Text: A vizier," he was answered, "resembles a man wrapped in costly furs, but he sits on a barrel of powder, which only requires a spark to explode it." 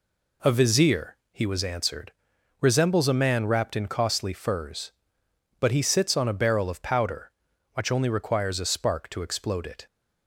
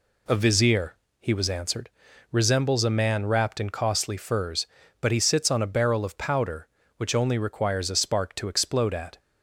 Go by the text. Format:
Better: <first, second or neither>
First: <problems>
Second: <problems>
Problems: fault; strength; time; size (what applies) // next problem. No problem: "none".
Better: first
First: none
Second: says "at" for "it"; at 8.9 s